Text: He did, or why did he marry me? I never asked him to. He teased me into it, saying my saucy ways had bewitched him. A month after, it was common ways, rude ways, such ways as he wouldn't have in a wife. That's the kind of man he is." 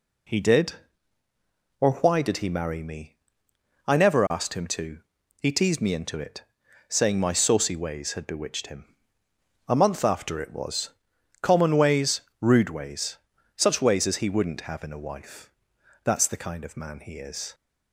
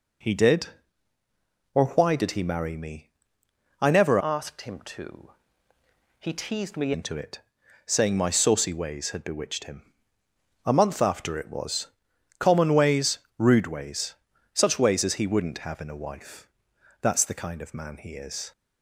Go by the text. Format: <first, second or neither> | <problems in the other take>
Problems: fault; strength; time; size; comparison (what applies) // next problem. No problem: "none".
first | changes voice from "asked" to "me"; from 4.2 to 6.9 s; 2.7 s long // pauses between "was" and "common"; noticeable; at 11.8 s; 0.50 s long; noticeable in the first